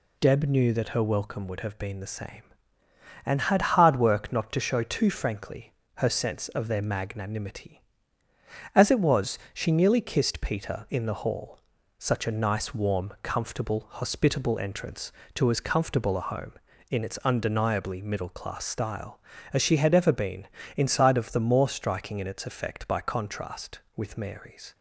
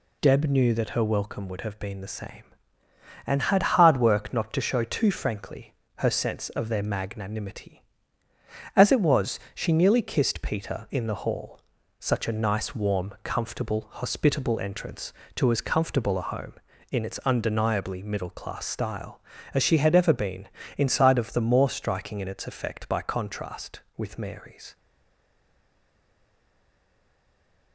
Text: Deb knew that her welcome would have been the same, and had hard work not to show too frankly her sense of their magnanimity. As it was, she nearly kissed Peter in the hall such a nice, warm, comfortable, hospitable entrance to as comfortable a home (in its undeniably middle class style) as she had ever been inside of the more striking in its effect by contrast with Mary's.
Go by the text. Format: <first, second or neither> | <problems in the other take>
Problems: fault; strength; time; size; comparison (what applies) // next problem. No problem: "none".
first | pauses between "frankly" and "her"; slight; at 5.7 s; 0.24 s long; slight in the first // pauses between "hall" and "such"; at 11.6 s; 0.40 s long; also in the first // pauses between "been" and "inside"; slight; at 20.4 s; 0.28 s long; slight in the first // stays silent after the last word; strong; from 24.7 s on; 3.0 s long